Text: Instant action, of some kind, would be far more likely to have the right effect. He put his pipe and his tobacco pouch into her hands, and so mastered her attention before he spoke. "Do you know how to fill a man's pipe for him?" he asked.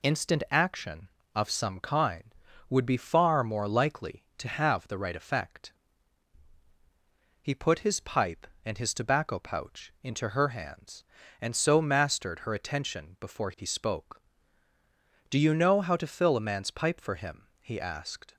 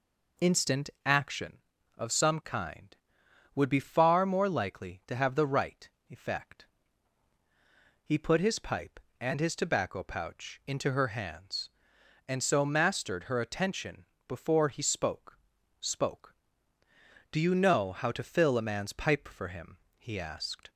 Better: first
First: none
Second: pauses between "right" and "effect"; slight; at 5.8 s; 0.20 s long // pauses between "attention" and "before"; slight; at 14.0 s; 0.22 s long // says "spoke" twice; at 15.8 s

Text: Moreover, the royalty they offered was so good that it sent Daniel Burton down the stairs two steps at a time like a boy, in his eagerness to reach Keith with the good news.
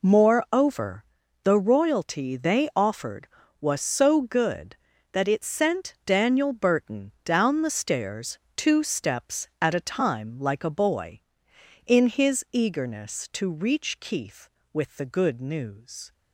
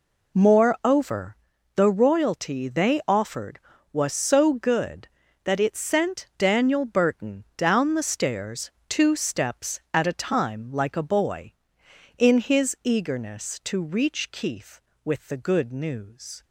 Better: neither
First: pauses between "stairs" and "two"; slight; at 8.3 s; 0.18 s long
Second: pauses between "stairs" and "two"; slight; at 8.7 s; 0.18 s long

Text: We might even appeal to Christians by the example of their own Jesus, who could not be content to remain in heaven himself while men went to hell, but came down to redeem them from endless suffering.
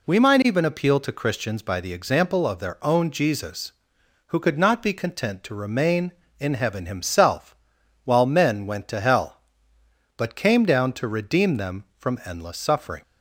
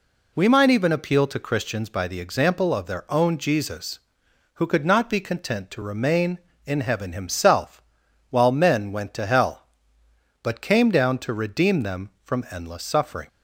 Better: neither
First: pauses between "himself" and "while"; noticeable; at 7.5 s; 0.48 s long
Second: pauses between "himself" and "while"; noticeable; at 7.8 s; 0.47 s long

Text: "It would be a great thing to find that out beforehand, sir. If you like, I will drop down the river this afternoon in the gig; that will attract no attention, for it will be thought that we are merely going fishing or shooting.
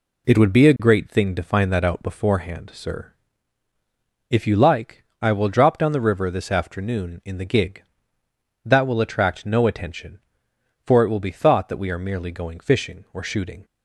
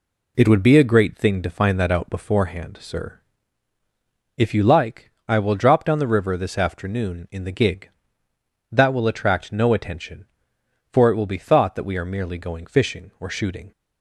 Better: neither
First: none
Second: none

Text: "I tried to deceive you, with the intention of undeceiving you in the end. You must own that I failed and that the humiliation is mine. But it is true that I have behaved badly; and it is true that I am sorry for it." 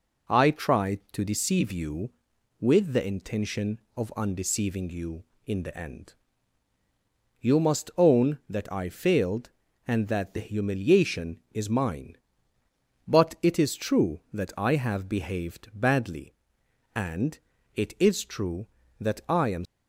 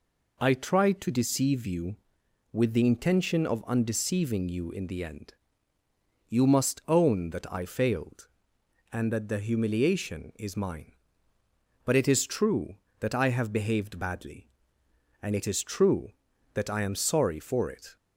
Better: second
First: pauses between "and" and "it"; slight; at 17.3 s; 0.34 s long // stops before "sorry for it"; at 19.6 s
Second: none

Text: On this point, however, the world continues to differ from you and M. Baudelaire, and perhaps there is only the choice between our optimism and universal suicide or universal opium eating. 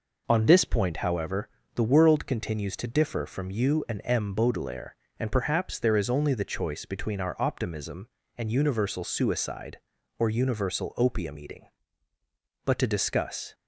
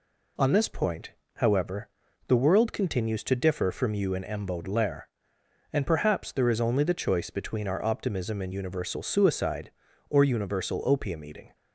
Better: second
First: goes on to say "But to discuss"; noticeable; from 12.6 s on; 0.90 s long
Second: none

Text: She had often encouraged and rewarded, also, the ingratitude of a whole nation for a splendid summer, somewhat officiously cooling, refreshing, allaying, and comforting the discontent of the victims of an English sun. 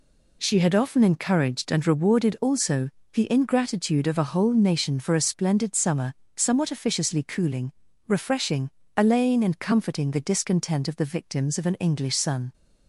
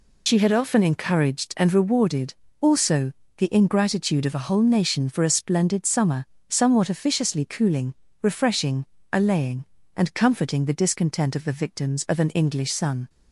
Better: first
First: none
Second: loses the start of "She"; at 0.2 s; 40 ms

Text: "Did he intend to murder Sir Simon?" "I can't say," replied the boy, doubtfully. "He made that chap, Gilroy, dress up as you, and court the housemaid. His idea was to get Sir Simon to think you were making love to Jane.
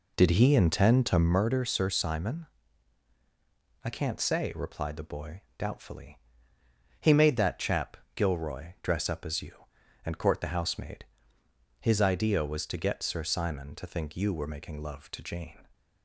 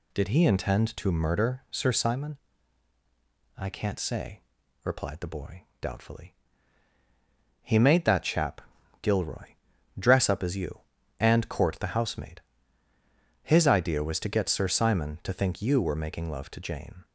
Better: second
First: starts louder than the rest; slight; until 1.4 s; 3.5 dB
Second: none

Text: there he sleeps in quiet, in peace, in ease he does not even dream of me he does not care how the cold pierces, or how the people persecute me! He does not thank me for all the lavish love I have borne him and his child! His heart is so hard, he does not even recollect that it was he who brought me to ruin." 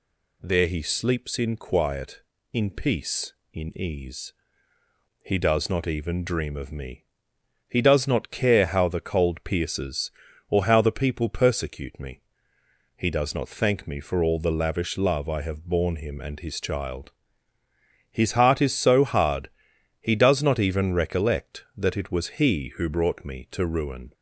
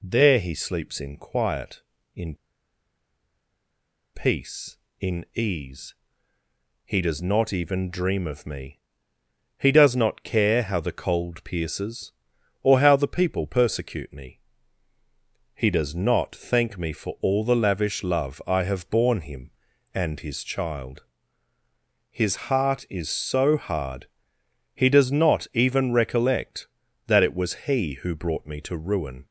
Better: first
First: pauses between "ease" and "he"; noticeable; at 4.3 s; 0.92 s long // pauses between "me" and "he"; noticeable; at 7.0 s; 0.62 s long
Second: pauses between "in" and "peace"; strong; at 2.3 s; 1.8 s long // pauses between "ease" and "he"; noticeable; at 5.9 s; 0.90 s long // pauses between "me" and "he"; noticeable; at 8.7 s; 0.78 s long

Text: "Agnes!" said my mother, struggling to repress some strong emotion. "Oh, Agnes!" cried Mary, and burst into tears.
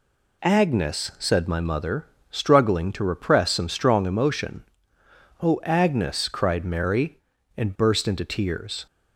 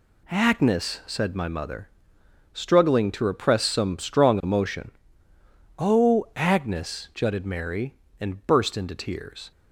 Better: first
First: none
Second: says "jutted" for "cried"; at 7.1 s

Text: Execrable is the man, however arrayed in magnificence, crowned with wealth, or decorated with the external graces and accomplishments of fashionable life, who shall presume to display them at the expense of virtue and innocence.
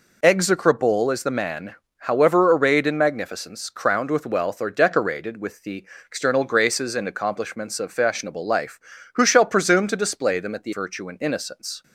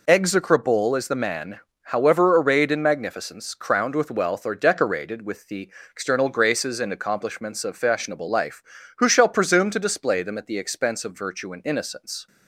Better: second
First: pauses between "the" and "external"; slight; at 5.8 s; 0.22 s long // skips "expense of"; at 10.7 s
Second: pauses between "the" and "external"; slight; at 5.7 s; 0.22 s long

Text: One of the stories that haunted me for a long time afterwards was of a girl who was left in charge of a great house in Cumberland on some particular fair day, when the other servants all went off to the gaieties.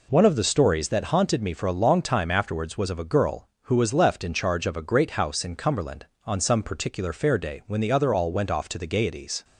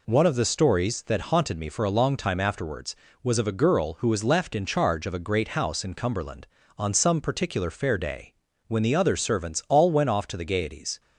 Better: second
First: skips "servants"; at 8.1 s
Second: none

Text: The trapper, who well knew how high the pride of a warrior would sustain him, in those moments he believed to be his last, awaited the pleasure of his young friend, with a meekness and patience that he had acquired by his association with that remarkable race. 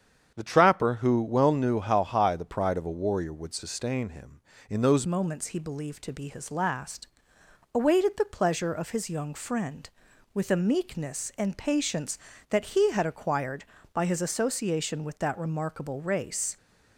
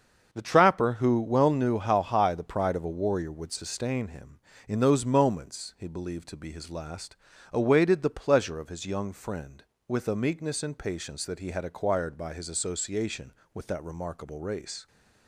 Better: second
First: starts louder than the rest; strong; until 1.3 s; 8 dB // changes voice at "moments"; from 5.0 s on; 11.5 s long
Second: starts louder than the rest; until 1.3 s; 6.5 dB

